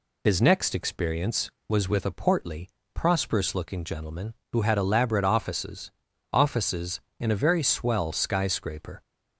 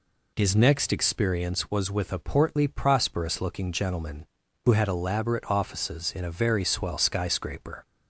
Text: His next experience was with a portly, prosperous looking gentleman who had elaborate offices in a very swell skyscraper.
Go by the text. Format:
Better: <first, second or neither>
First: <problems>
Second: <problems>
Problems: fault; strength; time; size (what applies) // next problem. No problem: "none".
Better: second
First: says "offices" twice; at 6.3 s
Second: none